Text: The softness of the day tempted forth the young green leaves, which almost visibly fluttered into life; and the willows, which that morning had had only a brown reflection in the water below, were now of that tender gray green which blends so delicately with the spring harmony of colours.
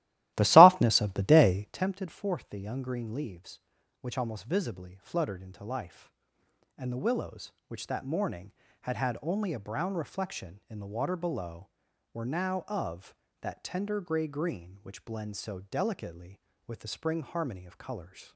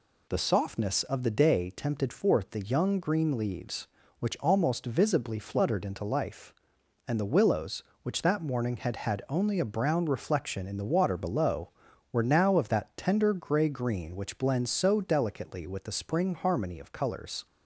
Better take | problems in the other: second | starts louder than the rest; strong; until 1.9 s; 15.5 dB

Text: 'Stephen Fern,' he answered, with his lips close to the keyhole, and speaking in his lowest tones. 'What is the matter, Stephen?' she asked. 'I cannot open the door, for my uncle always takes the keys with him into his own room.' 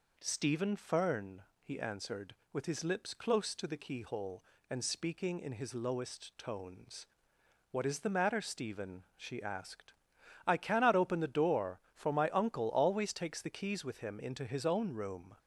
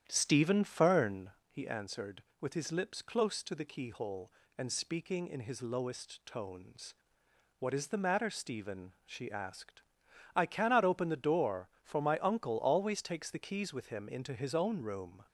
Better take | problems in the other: first | starts louder than the rest; strong; until 1.5 s; 9.5 dB

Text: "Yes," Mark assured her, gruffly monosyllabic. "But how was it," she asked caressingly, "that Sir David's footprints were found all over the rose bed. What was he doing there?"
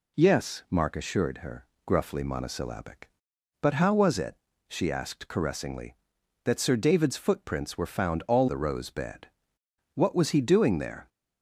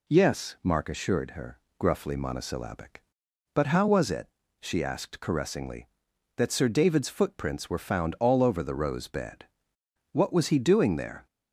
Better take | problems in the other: second | skips "over"; at 8.4 s

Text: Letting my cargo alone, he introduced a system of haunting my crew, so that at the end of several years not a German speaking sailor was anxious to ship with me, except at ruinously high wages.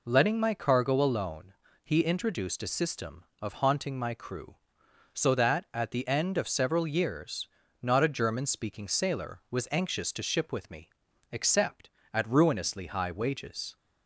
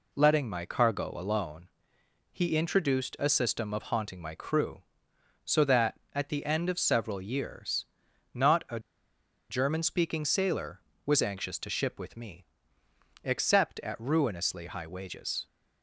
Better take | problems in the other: first | pauses between "years" and "not"; noticeable; at 7.8 s; 0.48 s long; slight in the first // pauses between "a" and "German"; noticeable; at 8.7 s; 0.69 s long

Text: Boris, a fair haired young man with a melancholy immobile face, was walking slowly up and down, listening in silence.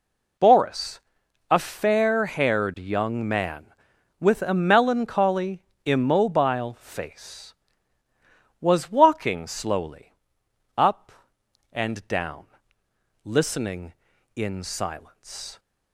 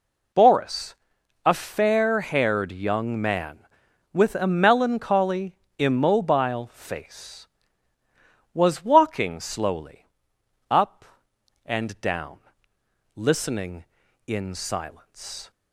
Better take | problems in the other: neither | pauses between "melancholy" and "immobile"; slight; the same in both // pauses between "slowly" and "up"; noticeable; the same in both

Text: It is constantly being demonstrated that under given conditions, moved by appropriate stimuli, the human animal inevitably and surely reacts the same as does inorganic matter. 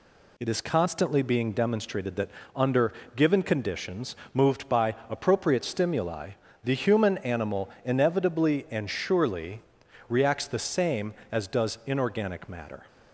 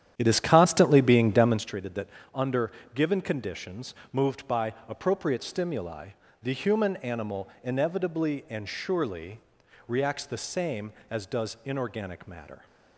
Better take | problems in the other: first | starts louder than the rest; strong; until 1.8 s; 10 dB // pauses between "that" and "under"; slight; at 2.0 s; 0.26 s long; slight in the first // pauses between "under" and "given"; slight; at 2.7 s; 0.22 s long; slight in the first // pauses between "surely" and "reacts"; noticeable; at 9.4 s; 0.46 s long; noticeable in the first

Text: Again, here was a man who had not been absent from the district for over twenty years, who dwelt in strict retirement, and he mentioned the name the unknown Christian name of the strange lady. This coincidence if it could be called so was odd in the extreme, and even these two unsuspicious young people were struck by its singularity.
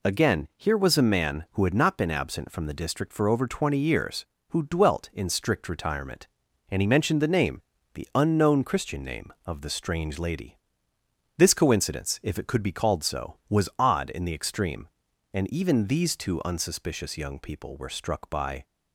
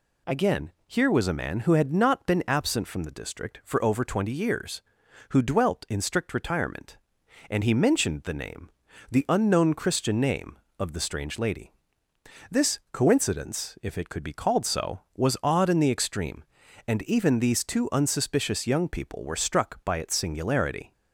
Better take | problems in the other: second | pauses between "name" and "the"; slight; at 7.6 s; 0.32 s long; also in the second // stops before "its singularity"; at 18.6 s

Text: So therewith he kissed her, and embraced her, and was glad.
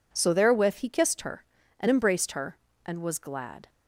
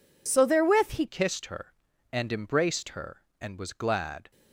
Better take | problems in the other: first | changes voice at "kissed"; from 1.0 s on; 3.3 s long

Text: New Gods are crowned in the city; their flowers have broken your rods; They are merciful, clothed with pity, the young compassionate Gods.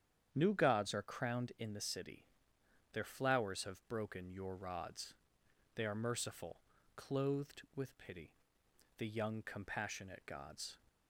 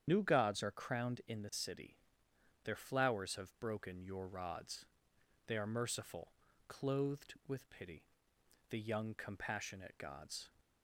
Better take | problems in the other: first | loses the start of "New"; at 0.0 s; 60 ms // starts louder than the rest; strong; until 1.0 s; 8.5 dB; strong in the first

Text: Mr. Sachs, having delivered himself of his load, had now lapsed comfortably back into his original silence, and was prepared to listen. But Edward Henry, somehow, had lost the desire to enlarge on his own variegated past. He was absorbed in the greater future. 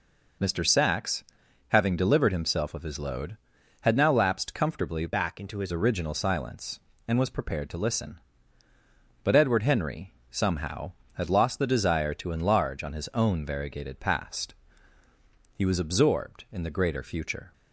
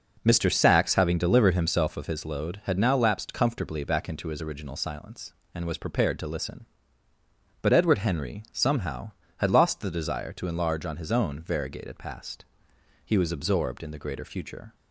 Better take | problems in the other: second | changes voice from "back" to "his"; from 5.0 to 5.7 s; 0.7 s long

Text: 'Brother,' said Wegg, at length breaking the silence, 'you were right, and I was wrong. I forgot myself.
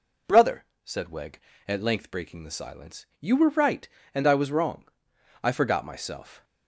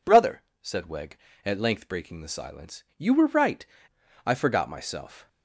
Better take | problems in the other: first | skips "and I was wrong"; at 3.9 s

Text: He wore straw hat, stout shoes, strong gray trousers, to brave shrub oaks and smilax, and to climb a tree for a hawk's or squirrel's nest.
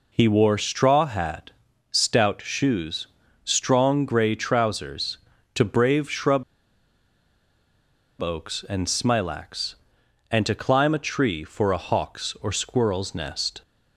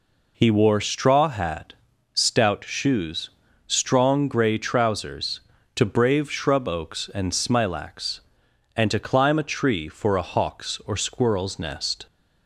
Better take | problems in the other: second | pauses between "shrub" and "oaks"; strong; at 6.4 s; 1.7 s long

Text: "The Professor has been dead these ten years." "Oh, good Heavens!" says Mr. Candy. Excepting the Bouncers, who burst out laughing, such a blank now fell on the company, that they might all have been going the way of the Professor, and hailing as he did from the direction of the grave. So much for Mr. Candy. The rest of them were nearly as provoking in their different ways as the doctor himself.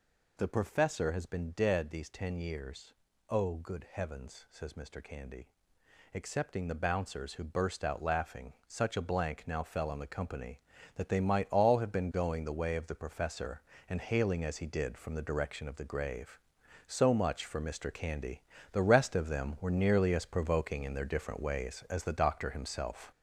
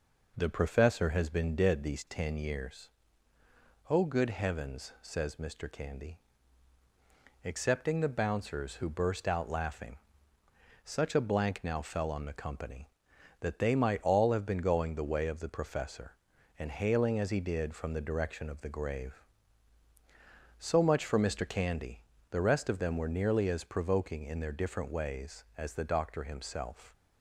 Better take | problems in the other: second | gets louder; noticeable; throughout; 6 dB

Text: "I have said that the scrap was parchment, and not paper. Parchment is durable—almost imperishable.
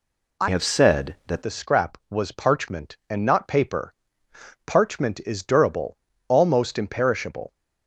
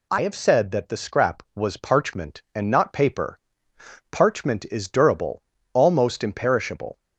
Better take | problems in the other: second | changes voice from "have" to "that"; from 0.4 to 1.4 s; 1.0 s long

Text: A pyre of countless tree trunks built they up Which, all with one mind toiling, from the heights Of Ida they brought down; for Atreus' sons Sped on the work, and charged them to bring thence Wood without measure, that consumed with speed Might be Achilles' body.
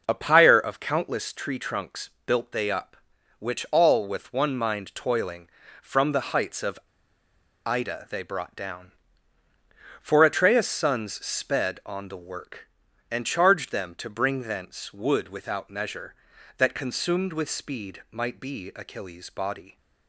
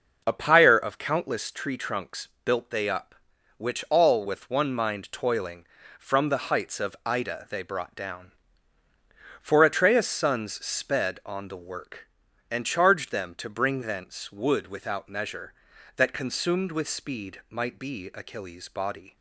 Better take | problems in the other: second | pauses between "trunks" and "built"; slight; at 2.0 s; 0.16 s long; slight in the second // pauses between "Of" and "Ida"; noticeable; at 6.7 s; 0.89 s long

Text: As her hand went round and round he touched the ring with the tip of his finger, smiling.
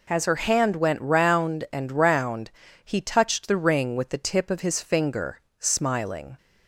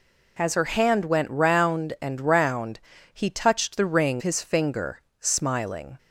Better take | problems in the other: first | pauses between "round" and "he"; slight; at 2.7 s; 0.32 s long; slight in the first // skips "with the tip of"; at 4.2 s

